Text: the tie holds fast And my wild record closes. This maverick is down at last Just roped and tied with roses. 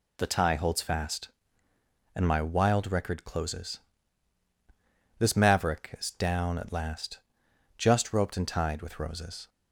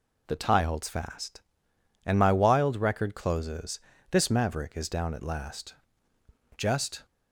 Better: first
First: pauses between "last" and "Just"; noticeable; at 7.1 s; 0.58 s long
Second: pauses between "last" and "Just"; noticeable; at 5.7 s; 0.82 s long // stops before "roped and tied with roses"; at 7.0 s

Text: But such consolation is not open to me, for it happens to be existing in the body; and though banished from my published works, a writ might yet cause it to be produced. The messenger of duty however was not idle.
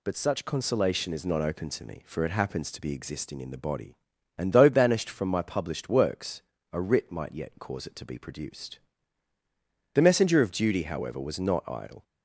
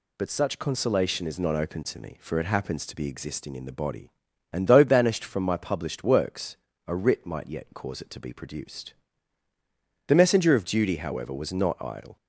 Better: neither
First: none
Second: none

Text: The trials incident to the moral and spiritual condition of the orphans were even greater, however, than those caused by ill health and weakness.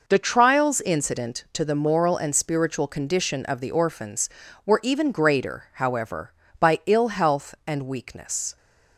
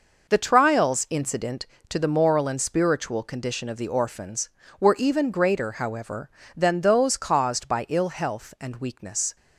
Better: second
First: skips "than those caused"; at 6.4 s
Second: none

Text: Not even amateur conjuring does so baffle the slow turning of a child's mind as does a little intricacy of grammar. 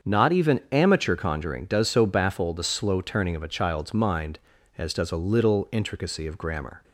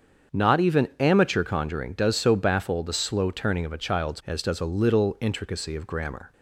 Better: first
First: starts louder than the rest; until 1.1 s; 7 dB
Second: starts louder than the rest; strong; until 1.4 s; 7 dB // skips "mind"; at 4.2 s

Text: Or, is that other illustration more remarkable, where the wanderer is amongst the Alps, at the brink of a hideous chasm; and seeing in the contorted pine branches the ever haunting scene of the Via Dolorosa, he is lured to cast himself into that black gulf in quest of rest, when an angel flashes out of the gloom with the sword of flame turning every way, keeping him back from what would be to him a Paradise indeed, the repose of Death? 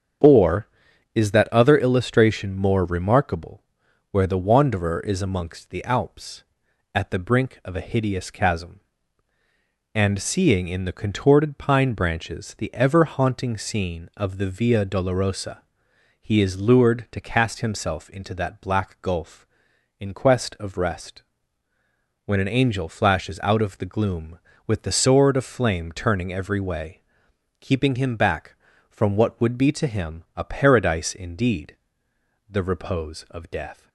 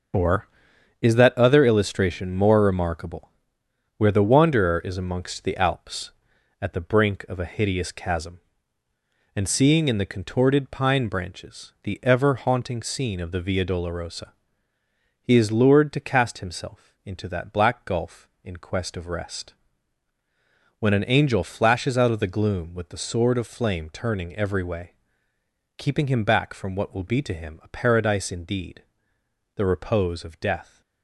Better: first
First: starts louder than the rest; strong; until 1.7 s; 7.5 dB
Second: starts louder than the rest; until 1.6 s; 6 dB // says "will" for "would"; at 26.9 s

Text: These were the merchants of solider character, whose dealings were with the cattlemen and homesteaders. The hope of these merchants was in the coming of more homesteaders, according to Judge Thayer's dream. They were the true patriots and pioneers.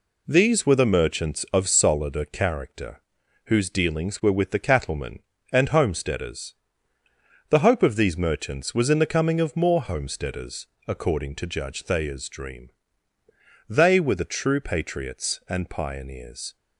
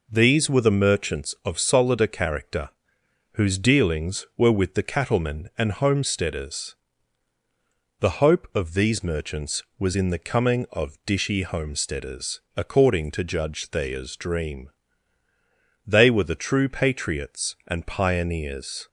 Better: first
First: none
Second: says "dishy" for "more"; at 11.0 s

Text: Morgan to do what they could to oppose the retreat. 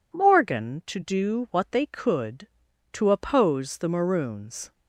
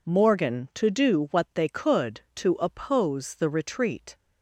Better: second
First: says "maroons" for "retreat"; at 3.8 s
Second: none

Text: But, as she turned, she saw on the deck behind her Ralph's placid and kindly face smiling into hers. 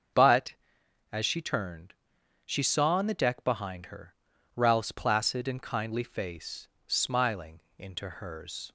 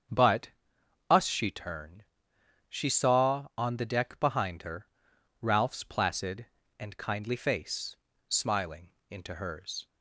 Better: first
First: starts louder than the rest; until 1.7 s; 7 dB // pauses between "her" and "Ralph's"; at 4.1 s; 0.42 s long // pauses between "face" and "smiling"; slight; at 6.6 s; 0.18 s long // pauses between "smiling" and "into"; slight; at 7.6 s; 0.18 s long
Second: starts louder than the rest; strong; until 1.7 s; 7.5 dB // says "us" for "as"; at 1.1 s // pauses between "her" and "Ralph's"; noticeable; at 4.8 s; 0.54 s long // pauses between "face" and "smiling"; slight; at 7.9 s; 0.34 s long // pauses between "smiling" and "into"; slight; at 8.9 s; 0.20 s long

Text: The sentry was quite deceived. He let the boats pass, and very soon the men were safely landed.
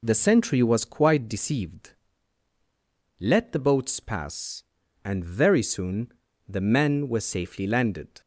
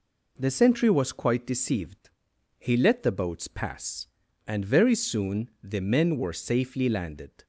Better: second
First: skips "He"; at 2.5 s // pauses between "soon" and "the"; slight; at 6.1 s; 0.34 s long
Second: none

